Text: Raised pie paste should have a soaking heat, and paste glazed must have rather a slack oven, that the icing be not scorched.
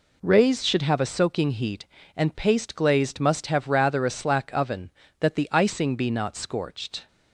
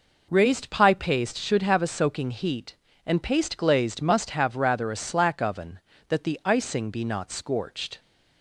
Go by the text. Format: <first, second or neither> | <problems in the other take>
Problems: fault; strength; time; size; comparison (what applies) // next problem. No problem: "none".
second | skips "pie paste"; at 0.6 s